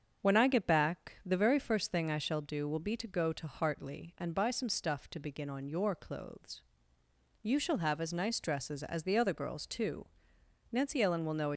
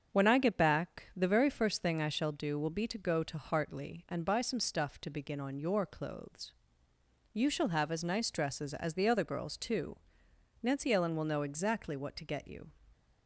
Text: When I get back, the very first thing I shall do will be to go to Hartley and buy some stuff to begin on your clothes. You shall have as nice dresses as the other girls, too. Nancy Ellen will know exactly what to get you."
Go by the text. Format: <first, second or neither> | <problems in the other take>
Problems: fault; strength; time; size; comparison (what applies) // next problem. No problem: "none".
second | starts louder than the rest; strong; until 1.3 s; 7 dB; strong in the second // stops before "exactly what to get you"; at 11.5 s